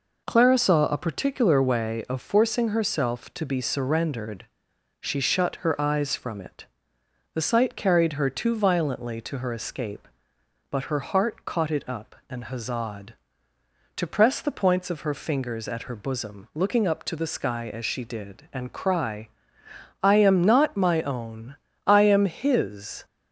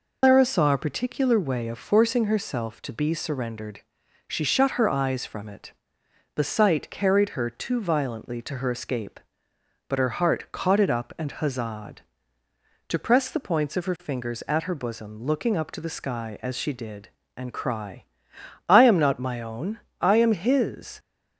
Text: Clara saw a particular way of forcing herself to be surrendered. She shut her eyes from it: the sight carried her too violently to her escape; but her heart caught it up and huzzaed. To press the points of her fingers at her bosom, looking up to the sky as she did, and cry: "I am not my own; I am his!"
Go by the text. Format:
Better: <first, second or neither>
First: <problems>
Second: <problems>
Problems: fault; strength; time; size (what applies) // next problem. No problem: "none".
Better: first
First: none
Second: loses the start of "Clara"; at 0.2 s; 155 ms